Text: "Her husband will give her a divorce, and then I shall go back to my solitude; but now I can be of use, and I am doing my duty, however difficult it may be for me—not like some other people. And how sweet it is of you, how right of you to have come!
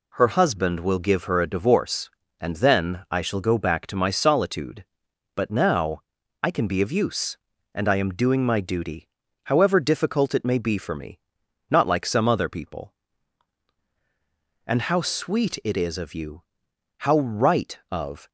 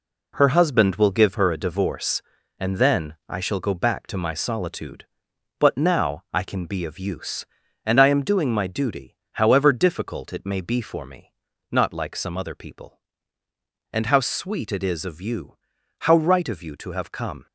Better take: second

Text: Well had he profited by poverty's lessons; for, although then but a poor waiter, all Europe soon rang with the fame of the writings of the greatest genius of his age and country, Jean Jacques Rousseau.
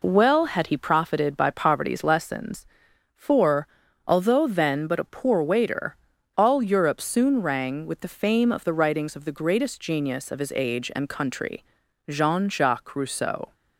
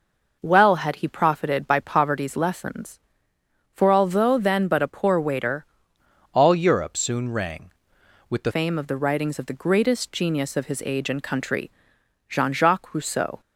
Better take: first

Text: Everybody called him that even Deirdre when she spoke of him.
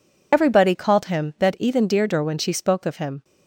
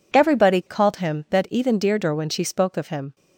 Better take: second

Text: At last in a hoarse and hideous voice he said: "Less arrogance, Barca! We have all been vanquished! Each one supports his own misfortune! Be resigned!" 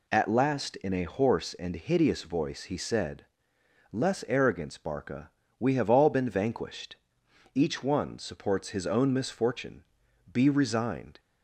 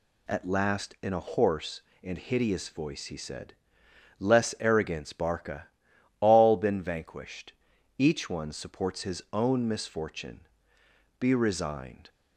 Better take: first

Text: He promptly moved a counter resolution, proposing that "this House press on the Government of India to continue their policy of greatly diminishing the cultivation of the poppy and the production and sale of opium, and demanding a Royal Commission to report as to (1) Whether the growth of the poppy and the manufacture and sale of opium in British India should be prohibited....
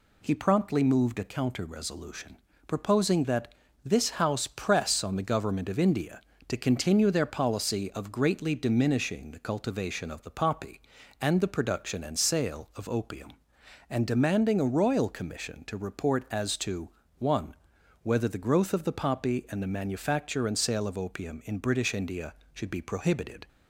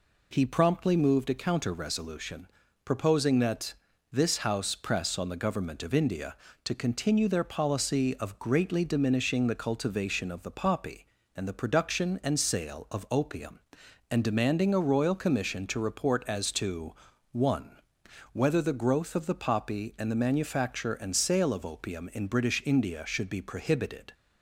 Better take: neither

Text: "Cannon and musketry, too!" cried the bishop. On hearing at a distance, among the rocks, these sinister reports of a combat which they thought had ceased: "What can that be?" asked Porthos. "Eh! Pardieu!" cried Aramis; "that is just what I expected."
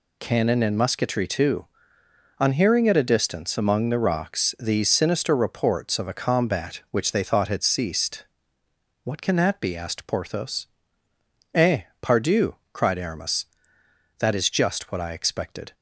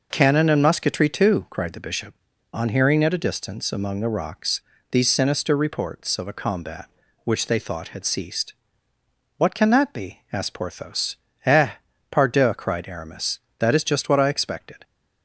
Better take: second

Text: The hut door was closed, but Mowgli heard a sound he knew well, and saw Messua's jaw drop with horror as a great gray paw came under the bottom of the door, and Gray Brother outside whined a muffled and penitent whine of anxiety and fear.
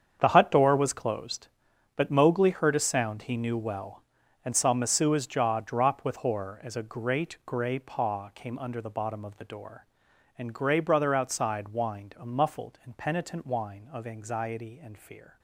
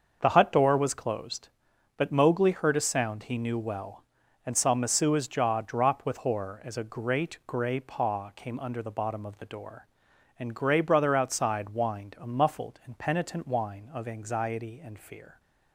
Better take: second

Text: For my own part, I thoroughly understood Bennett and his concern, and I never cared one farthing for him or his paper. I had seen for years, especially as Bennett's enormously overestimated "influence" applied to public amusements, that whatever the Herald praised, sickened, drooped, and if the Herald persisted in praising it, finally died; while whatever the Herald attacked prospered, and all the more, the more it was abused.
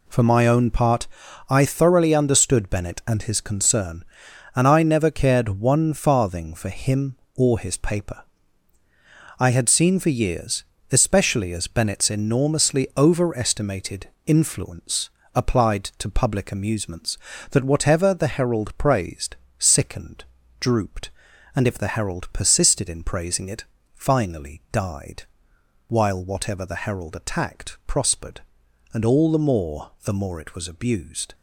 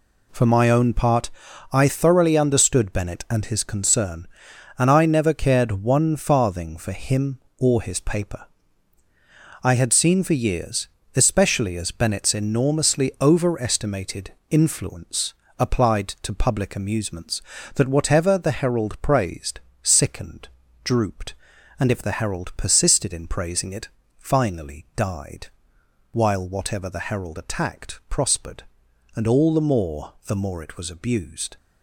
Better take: neither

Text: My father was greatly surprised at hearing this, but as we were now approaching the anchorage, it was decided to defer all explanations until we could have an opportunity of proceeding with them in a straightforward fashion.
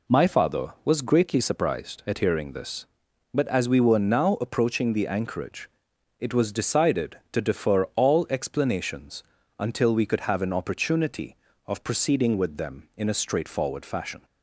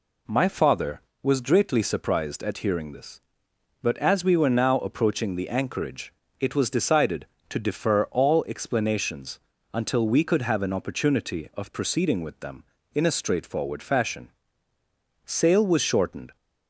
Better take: first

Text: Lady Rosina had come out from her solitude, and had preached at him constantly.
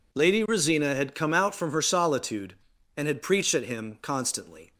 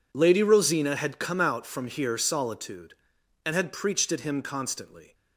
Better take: first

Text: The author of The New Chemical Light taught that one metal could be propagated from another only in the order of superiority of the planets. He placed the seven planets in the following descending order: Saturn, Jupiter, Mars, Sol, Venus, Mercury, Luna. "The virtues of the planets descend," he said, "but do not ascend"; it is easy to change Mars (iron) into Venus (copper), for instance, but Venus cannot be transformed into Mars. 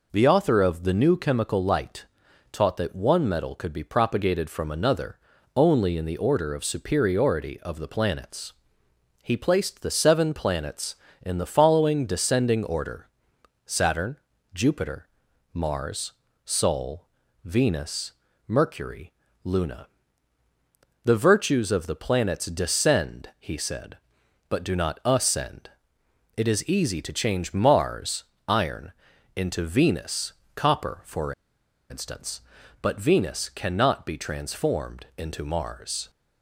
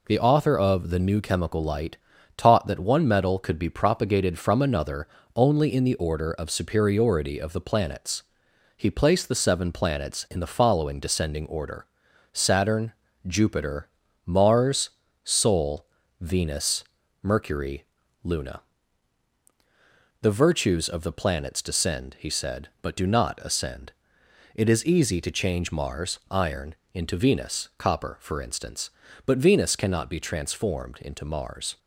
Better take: second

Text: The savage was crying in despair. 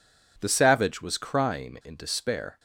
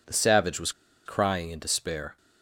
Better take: first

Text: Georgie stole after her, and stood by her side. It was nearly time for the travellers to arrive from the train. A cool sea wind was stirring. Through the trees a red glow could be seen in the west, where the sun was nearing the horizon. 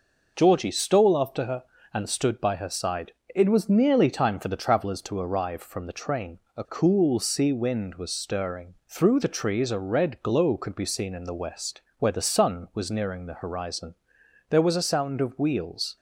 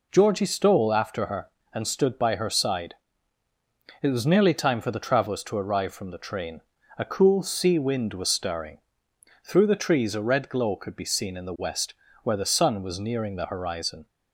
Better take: second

